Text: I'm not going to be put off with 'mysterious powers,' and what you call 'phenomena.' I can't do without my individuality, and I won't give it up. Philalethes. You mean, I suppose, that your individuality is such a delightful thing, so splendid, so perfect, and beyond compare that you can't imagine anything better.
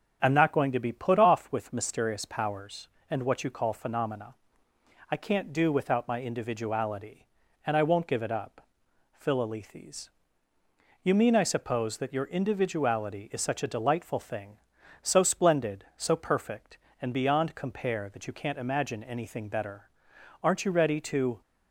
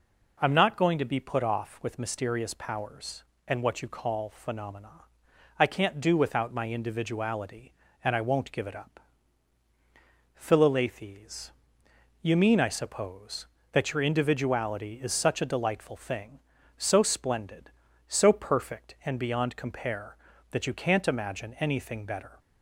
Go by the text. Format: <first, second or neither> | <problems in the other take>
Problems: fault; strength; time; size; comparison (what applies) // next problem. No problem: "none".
second | starts louder than the rest; strong; until 1.2 s; 8 dB // goes on to say "Aren't you ready to"; noticeable; from 20.4 s on; 0.98 s long